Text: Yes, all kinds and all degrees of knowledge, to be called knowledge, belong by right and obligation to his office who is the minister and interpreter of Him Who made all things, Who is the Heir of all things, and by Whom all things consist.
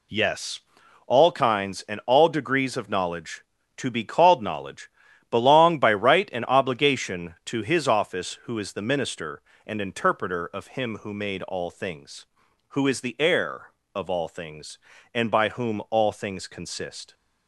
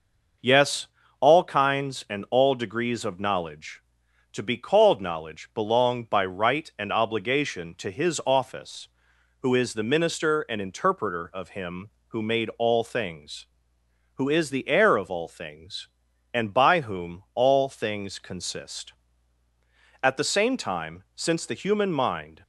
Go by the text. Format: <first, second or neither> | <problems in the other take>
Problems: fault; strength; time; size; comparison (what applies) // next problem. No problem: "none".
first | goes on to say "At the same time since the human mind"; strong; from 20.0 s on; 2.4 s long